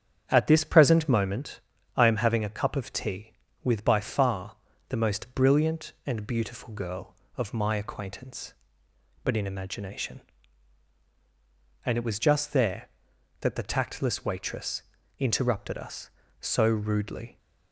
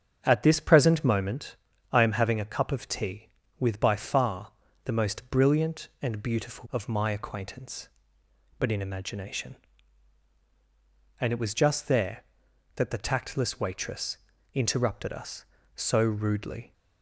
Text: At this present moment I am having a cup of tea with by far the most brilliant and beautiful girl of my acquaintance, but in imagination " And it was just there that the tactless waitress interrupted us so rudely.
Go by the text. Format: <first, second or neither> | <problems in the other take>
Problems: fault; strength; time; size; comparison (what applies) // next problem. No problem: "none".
first | starts louder than the rest; strong; until 1.2 s; 9 dB; strong in the first // pauses between "moment" and "I"; slight; at 1.5 s; 0.36 s long; slight in the first // pauses between "far" and "the"; slight; at 4.5 s; 0.32 s long; slight in the first // skips "girl"; at 6.6 s // pauses between "waitress" and "interrupted"; at 14.1 s; 0.38 s long; also in the first